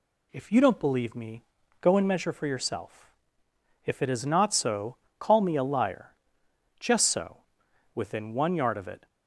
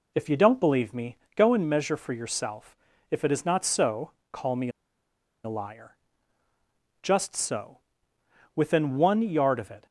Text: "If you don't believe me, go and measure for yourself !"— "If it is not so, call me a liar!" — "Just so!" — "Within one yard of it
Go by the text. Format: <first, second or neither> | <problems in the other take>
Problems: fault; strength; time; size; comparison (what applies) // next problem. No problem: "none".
first | pauses between "me" and "a"; noticeable; at 4.6 s; 0.75 s long